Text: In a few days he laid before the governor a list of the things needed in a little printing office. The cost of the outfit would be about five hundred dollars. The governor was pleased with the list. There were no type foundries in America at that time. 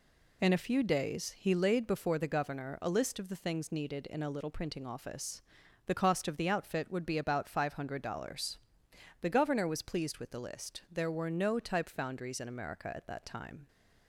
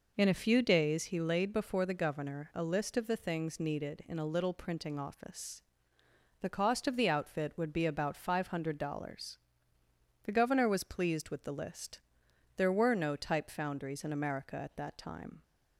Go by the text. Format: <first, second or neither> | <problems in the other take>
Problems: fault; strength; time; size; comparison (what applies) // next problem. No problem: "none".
first | starts louder than the rest; noticeable; until 1.3 s; 5 dB